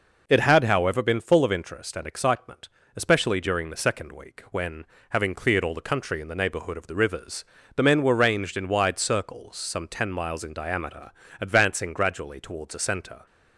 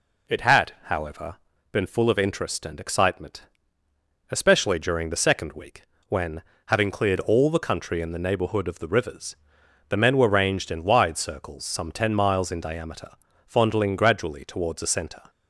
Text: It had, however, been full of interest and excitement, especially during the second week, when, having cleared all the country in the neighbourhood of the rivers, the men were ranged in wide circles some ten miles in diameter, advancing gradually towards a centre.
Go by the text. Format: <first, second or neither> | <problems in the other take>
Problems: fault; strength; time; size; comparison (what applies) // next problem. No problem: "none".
first | says "fondling" for "advancing"; at 13.4 s